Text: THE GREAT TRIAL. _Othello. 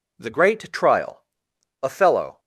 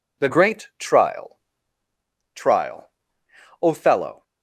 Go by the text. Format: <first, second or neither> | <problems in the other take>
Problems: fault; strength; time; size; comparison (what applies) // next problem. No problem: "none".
first | says "TRIAL" twice; at 2.3 s